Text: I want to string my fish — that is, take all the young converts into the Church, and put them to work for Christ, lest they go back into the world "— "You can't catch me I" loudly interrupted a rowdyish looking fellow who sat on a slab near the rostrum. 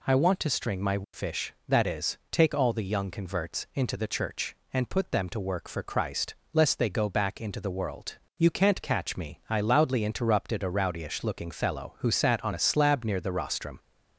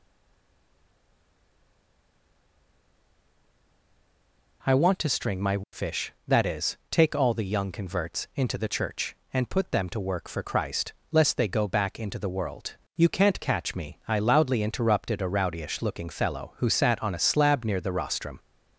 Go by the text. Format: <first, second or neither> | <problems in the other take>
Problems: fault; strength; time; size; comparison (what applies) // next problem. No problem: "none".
first | stays silent before the first word; strong; until 4.6 s; 4.6 s long